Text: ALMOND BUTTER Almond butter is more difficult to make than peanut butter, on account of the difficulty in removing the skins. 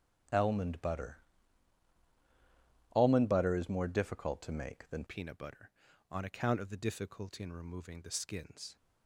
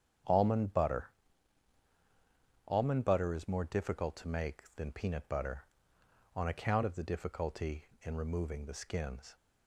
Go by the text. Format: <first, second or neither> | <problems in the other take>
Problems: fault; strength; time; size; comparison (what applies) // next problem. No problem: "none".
second | starts louder than the rest; strong; until 3.1 s; 10 dB; strong in the second // pauses between "BUTTER" and "Almond"; strong; at 1.1 s; 1.7 s long; strong in the second // changes voice at "peanut"; from 5.0 s on; 3.7 s long